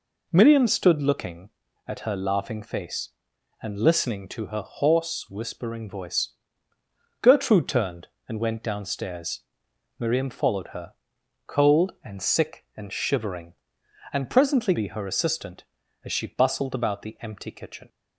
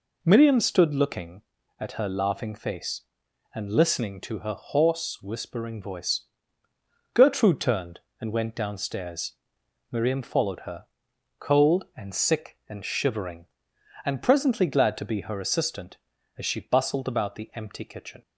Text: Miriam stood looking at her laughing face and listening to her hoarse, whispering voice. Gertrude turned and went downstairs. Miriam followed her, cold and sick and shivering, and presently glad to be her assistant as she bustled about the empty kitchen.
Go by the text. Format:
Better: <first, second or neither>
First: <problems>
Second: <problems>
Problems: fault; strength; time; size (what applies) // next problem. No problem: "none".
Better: second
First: skips "glad to"; at 14.7 s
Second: none